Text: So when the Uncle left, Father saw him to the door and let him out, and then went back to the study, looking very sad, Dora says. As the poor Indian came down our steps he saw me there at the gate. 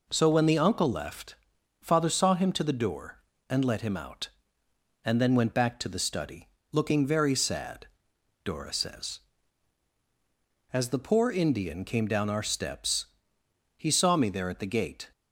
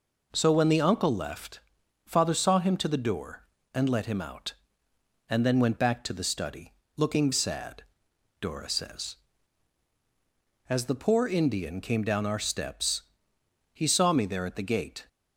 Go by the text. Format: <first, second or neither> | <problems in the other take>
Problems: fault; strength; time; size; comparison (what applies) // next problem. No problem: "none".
first | skips "very"; at 7.3 s // pauses between "steps" and "he"; noticeable; at 13.0 s; 0.72 s long; noticeable in the first